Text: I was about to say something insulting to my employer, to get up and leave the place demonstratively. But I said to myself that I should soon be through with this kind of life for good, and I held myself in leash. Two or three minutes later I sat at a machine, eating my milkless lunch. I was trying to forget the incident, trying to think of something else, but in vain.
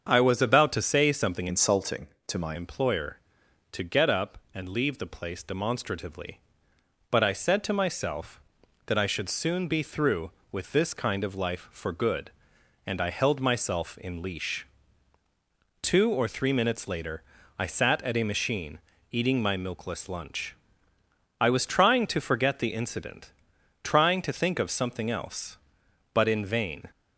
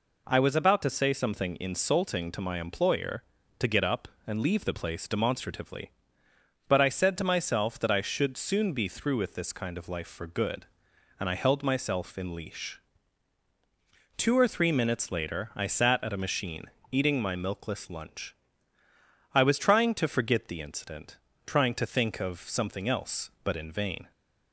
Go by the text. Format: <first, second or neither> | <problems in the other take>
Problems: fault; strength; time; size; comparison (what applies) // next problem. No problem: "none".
second | starts louder than the rest; until 1.1 s; 7 dB // changes voice from "insulting" to "my"; from 1.4 to 2.5 s; 1.1 s long // pauses between "later" and "I"; at 17.2 s; 0.38 s long